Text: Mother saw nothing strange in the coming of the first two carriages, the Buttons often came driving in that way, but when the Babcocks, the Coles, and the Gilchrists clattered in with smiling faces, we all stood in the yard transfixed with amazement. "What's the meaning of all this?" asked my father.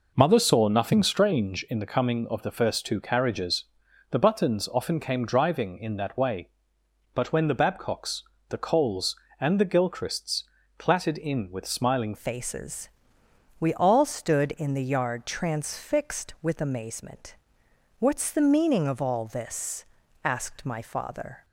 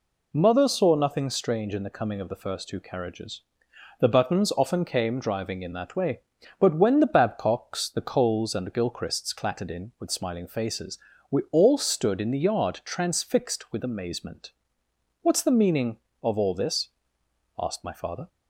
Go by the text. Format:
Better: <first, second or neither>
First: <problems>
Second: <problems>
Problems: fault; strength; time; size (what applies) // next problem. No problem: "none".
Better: second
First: pauses between "Gilchrists" and "clattered"; slight; at 10.4 s; 0.34 s long // changes voice at "faces"; from 12.1 s on; 9.3 s long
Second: none